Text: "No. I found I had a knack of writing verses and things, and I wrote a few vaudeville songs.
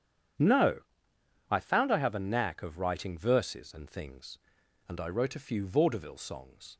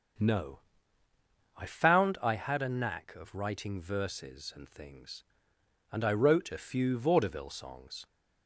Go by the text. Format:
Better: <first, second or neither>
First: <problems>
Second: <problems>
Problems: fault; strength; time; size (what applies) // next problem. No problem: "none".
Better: second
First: starts louder than the rest; strong; until 2.0 s; 9 dB // says "have" for "had"; at 1.9 s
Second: starts louder than the rest; noticeable; until 2.1 s; 6 dB